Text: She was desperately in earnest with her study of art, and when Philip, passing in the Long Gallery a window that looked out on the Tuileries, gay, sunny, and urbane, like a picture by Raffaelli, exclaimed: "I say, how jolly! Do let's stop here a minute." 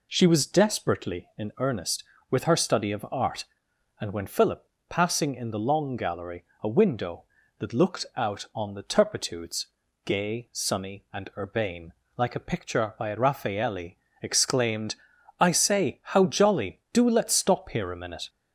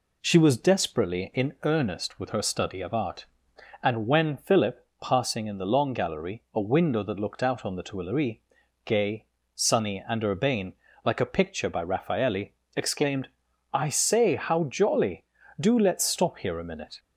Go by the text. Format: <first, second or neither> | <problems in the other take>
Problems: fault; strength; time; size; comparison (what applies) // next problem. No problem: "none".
second | pauses between "Gallery" and "a"; slight; at 6.4 s; 0.22 s long // says "Turpitudes" for "Tuileries"; at 8.8 s